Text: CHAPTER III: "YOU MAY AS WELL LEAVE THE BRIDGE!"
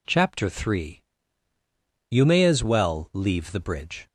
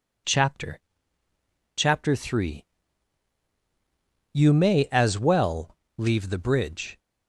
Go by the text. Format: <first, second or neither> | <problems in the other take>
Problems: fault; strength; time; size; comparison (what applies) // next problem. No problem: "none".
first | says "CHAPTER" twice; at 1.7 s // pauses between "WELL" and "LEAVE"; slight; at 5.7 s; 0.22 s long